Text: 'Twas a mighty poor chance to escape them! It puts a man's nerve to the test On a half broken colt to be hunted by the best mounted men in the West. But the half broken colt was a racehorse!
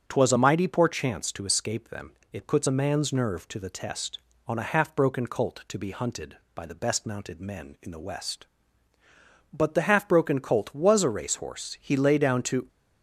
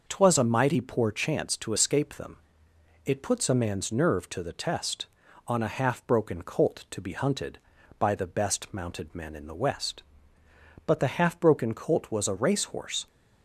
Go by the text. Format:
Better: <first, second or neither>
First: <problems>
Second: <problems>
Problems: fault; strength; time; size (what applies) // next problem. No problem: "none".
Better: second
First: starts louder than the rest; strong; until 1.0 s; 8 dB // goes on to say "He lay down to"; noticeable; from 11.7 s on; 0.88 s long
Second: none